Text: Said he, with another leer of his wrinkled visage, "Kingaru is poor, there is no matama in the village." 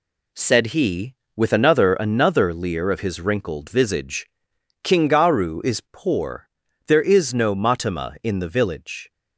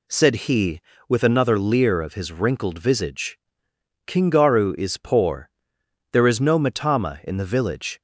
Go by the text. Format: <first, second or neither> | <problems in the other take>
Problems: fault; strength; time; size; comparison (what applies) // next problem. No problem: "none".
second | says "another" twice; at 1.9 s